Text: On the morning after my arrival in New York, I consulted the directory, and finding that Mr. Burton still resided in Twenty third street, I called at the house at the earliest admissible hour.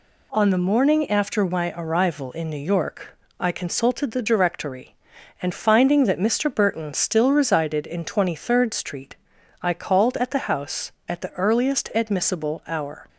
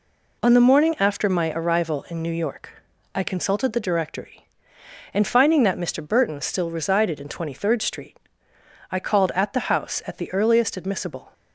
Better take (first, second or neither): first